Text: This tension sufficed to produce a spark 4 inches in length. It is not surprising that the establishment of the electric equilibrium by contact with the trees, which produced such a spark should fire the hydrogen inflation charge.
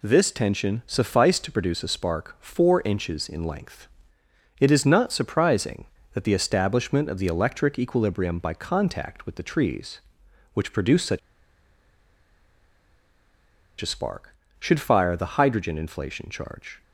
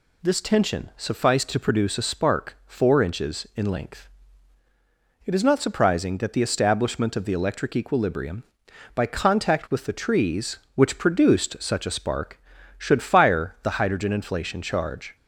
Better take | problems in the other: second | pauses between "such" and "a"; strong; at 11.1 s; 2.6 s long

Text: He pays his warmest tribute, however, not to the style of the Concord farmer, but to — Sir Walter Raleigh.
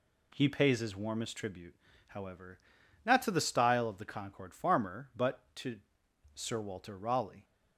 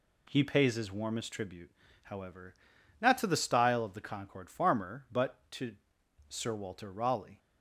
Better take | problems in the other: neither | none

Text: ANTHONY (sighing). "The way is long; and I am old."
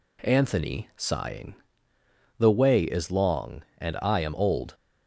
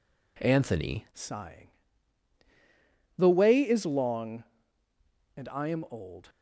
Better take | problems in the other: first | changes voice at "sighing"; from 1.1 s on; 5.1 s long

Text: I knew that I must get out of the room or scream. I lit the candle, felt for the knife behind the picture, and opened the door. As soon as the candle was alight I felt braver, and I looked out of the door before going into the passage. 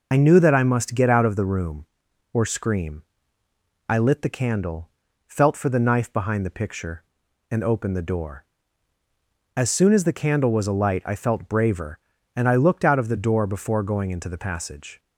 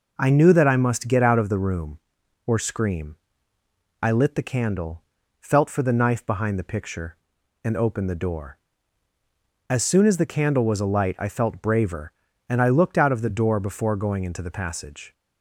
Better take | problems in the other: second | loses the start of "I"; at 0.1 s; 60 ms

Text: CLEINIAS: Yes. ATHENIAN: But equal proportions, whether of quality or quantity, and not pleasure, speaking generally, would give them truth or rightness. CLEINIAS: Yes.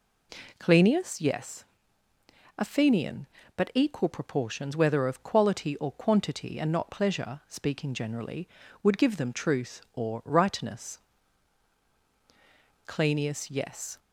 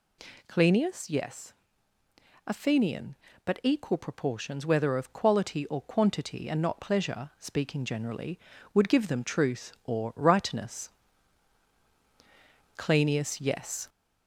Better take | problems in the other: first | gets louder; slight; throughout; 2.5 dB

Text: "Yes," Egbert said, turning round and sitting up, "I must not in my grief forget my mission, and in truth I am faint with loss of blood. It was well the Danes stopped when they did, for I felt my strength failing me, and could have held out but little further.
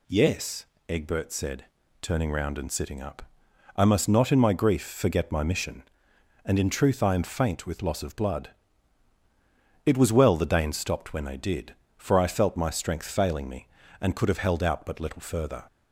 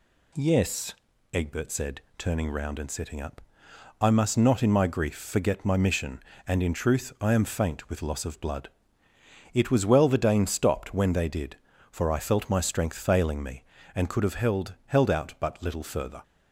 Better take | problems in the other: first | says "held" twice; at 14.8 s

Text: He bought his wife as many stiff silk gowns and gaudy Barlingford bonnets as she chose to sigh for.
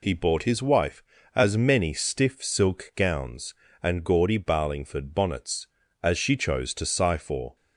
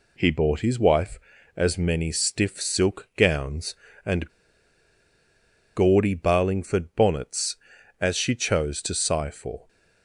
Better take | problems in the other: first | pauses between "and" and "gaudy"; strong; at 4.2 s; 1.4 s long

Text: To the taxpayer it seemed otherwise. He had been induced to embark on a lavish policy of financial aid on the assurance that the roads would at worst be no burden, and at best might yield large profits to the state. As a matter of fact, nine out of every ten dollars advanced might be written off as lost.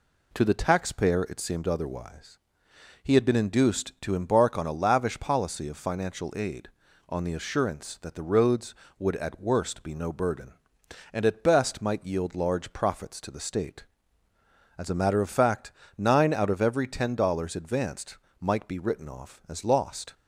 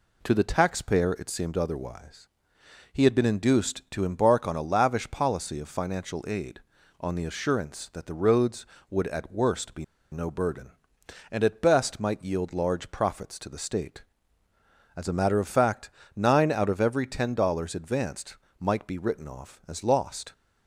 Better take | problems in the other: first | pauses between "be" and "no"; slight; at 9.8 s; 0.27 s long // pauses between "advanced" and "might"; slight; at 18.3 s; 0.22 s long; slight in the first

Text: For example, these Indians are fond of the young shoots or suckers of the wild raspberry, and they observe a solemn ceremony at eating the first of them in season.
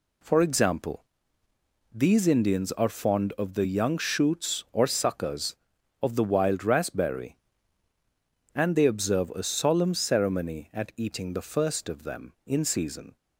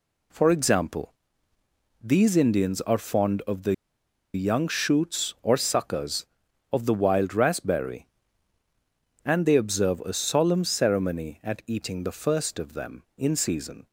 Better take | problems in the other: first | pauses between "the" and "young"; noticeable; at 3.7 s; 0.59 s long

